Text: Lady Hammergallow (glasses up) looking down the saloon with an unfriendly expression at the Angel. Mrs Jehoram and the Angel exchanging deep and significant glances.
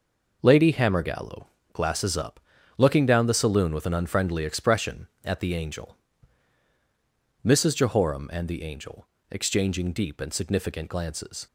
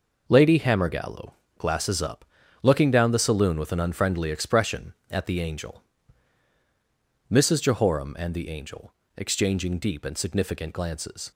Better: neither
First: pauses between "Angel" and "exchanging"; slight; at 9.0 s; 0.24 s long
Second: pauses between "Angel" and "exchanging"; slight; at 8.9 s; 0.24 s long

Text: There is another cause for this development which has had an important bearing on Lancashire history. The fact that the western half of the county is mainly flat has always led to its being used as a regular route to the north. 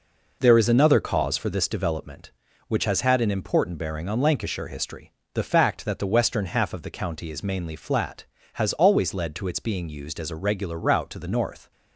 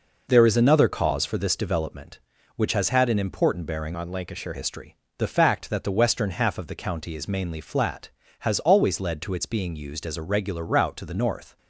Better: first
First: none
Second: changes voice from "on" to "Lancashire"; from 3.9 to 4.5 s; 0.6 s long

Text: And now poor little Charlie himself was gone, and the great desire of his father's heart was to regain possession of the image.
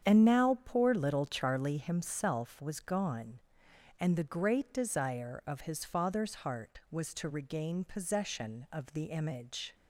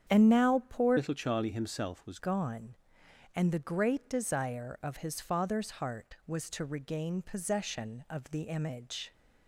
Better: first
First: starts louder than the rest; strong; until 1.1 s; 8.5 dB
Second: starts louder than the rest; strong; until 1.1 s; 8.5 dB // changes voice from "little" to "was"; from 0.9 to 2.1 s; 1.2 s long

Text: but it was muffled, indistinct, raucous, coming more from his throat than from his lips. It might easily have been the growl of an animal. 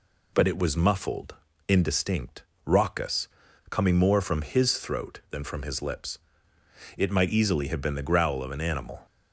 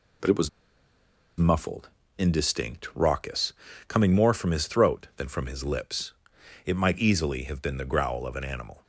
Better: first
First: none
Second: pauses between "was" and "muffled"; noticeable; at 0.4 s; 0.89 s long

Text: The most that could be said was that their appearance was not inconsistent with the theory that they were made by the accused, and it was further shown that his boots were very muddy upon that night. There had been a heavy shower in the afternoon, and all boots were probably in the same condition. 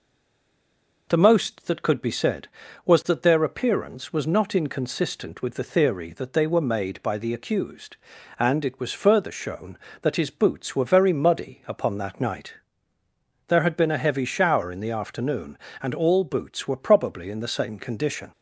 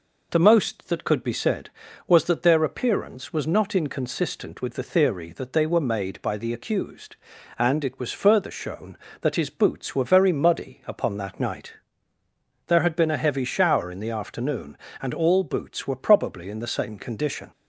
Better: second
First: stays silent before the first word; until 1.0 s; 1.0 s long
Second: none

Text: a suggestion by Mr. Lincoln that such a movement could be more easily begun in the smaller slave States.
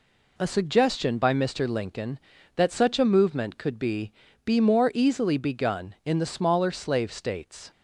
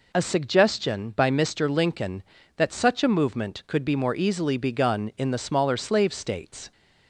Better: second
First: says "be" twice; at 4.4 s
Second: none

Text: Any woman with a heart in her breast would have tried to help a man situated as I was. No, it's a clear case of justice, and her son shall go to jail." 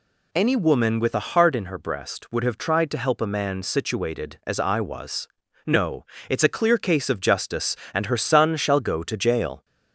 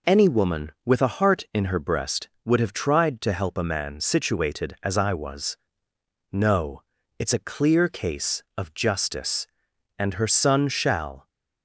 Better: first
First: none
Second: stops before "go to jail"; at 11.2 s

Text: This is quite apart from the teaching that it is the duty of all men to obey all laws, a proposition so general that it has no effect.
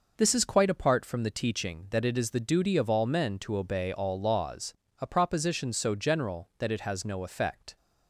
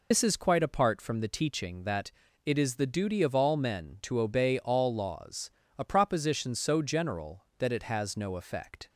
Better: first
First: none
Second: loses the start of "This"; at 0.1 s; 80 ms // pauses between "that" and "it"; slight; at 2.1 s; 0.36 s long

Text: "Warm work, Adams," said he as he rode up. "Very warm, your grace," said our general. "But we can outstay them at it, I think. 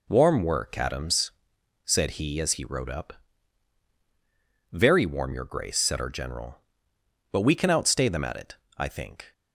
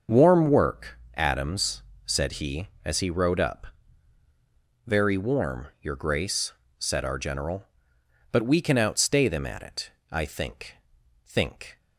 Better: first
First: none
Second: starts louder than the rest; until 1.2 s; 6.5 dB // says "think" twice; at 11.2 s

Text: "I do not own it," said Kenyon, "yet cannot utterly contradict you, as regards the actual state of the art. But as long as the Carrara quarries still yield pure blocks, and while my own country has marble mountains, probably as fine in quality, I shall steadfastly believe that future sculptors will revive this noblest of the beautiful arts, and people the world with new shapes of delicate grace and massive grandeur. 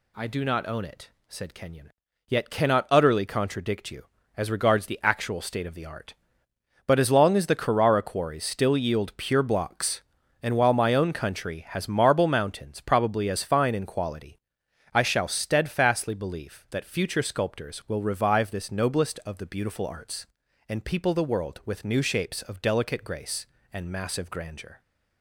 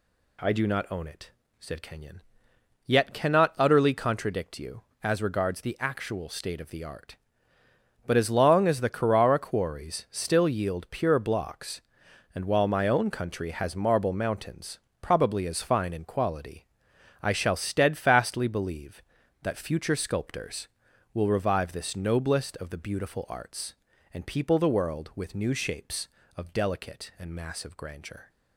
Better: first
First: none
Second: skips "grace"; at 27.1 s

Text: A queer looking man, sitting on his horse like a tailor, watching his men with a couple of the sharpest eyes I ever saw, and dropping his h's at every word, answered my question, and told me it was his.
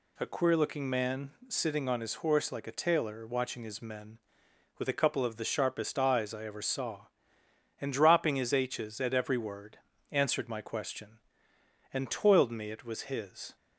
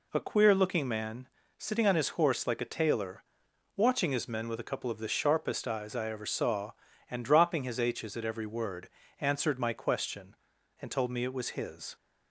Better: second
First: says "toiled" for "told"; at 12.0 s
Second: none

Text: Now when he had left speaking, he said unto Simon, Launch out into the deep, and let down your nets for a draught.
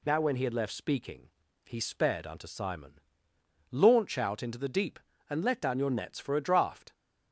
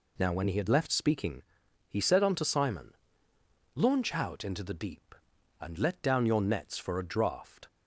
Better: second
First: says "sped" for "said"; at 1.8 s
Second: none

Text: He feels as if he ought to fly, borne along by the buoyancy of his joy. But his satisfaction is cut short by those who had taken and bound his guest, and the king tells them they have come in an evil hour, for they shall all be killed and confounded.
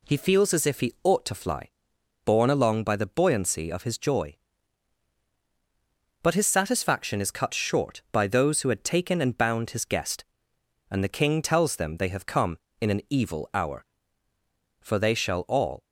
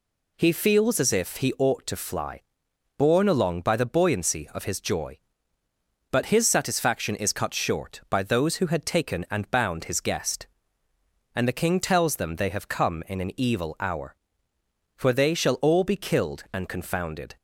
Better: second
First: stops before "be killed and confounded"; at 15.8 s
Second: none

